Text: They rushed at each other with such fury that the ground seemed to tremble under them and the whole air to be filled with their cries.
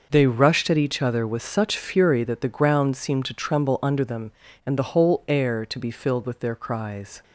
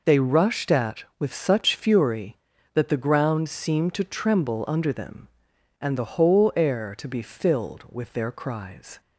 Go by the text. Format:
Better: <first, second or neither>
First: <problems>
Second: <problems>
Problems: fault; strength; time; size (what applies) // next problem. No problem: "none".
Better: first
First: none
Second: skips "each other"; at 1.1 s